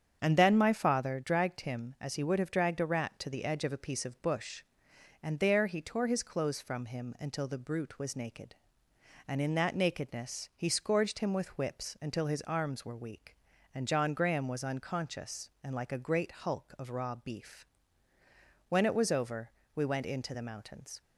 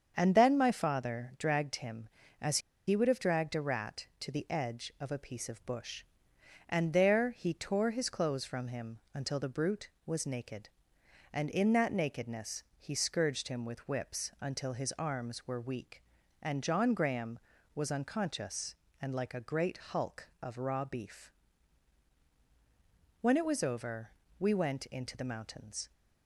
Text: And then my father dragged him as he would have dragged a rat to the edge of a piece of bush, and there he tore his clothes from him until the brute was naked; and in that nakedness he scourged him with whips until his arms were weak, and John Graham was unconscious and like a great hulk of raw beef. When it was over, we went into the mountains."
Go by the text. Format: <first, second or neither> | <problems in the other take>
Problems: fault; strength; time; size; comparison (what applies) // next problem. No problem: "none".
first | starts louder than the rest; strong; until 1.1 s; 7 dB; strong in the first // pauses between "as" and "he"; slight; at 2.5 s; 0.28 s long